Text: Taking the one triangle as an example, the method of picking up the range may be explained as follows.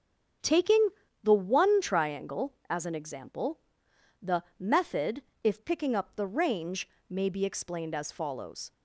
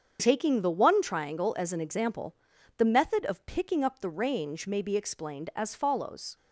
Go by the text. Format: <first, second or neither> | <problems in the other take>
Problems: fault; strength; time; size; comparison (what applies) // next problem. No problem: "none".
second | starts louder than the rest; strong; until 1.7 s; 7 dB; strong in the second // pauses between "Taking" and "the"; slight; at 0.8 s; 0.34 s long // pauses between "the" and "method"; slight; at 4.4 s; 0.16 s long // says "if" for "of"; at 5.4 s // pauses between "range" and "may"; slight; at 6.8 s; 0.20 s long